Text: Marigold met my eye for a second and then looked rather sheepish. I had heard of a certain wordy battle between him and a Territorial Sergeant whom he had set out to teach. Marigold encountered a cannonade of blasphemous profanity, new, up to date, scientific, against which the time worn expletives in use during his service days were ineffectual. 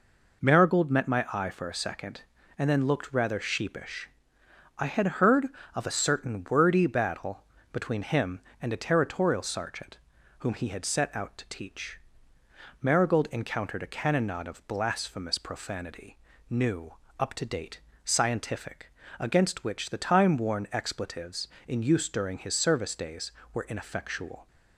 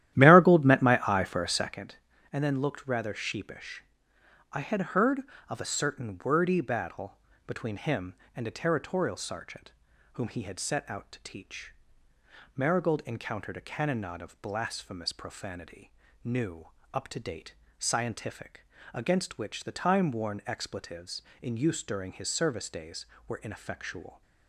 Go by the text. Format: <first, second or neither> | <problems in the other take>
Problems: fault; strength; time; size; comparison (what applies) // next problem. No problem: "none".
first | starts louder than the rest; strong; until 1.9 s; 12.5 dB // pauses between "battle" and "between"; slight; at 7.1 s; 0.26 s long; slight in the first // pauses between "Sergeant" and "whom"; at 9.7 s; 0.42 s long; also in the first